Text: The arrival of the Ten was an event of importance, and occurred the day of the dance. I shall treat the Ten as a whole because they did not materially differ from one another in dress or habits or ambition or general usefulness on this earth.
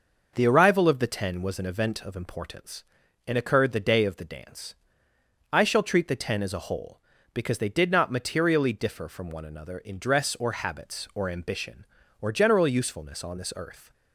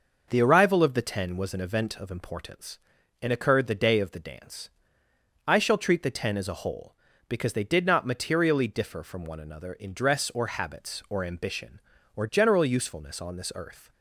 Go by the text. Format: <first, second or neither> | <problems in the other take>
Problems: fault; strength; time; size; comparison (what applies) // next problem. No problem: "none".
neither | none